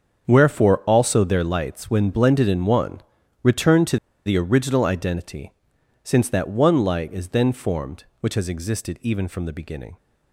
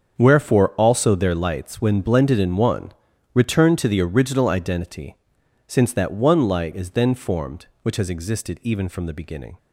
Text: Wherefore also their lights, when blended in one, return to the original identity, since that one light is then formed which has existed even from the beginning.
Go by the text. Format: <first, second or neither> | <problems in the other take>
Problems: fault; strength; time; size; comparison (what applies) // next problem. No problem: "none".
second | starts louder than the rest; until 1.2 s; 7 dB; also in the second // pauses between "to" and "the"; slight; at 3.9 s; 0.28 s long